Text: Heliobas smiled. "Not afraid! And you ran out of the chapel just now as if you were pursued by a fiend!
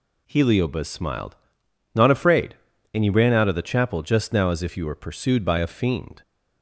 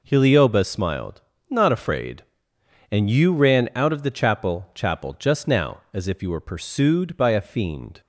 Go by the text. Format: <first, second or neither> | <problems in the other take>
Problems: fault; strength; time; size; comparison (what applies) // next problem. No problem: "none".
first | says "chapel" twice; at 4.7 s